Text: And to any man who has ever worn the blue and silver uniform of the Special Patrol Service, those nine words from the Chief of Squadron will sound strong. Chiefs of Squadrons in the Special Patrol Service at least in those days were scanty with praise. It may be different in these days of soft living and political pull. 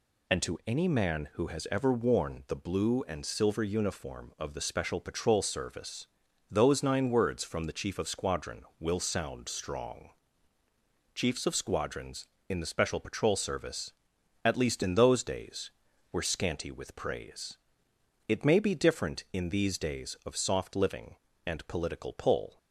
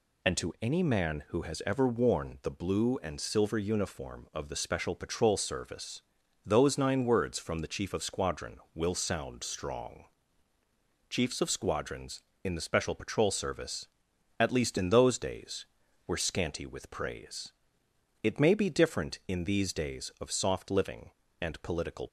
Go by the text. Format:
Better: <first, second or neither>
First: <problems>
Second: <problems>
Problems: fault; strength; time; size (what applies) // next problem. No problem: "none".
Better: first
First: none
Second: stops before "pull"; at 22.0 s